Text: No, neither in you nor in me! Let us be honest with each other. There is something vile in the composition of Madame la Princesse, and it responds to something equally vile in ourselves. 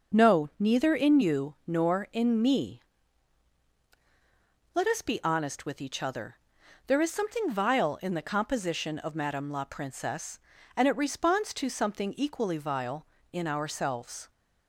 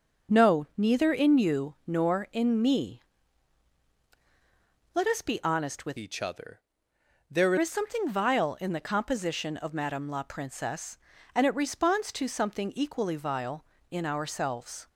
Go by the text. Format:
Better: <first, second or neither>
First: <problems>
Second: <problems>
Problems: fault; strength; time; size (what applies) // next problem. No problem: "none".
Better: first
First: none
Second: changes voice from "each" to "There"; from 5.9 to 7.5 s; 1.6 s long